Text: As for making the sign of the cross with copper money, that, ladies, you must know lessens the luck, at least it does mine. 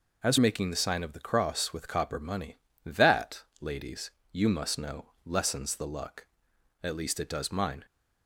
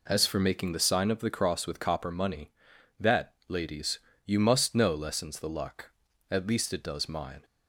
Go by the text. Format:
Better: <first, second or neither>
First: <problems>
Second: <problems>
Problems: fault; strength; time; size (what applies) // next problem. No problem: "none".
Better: second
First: skips "for"; at 0.3 s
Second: none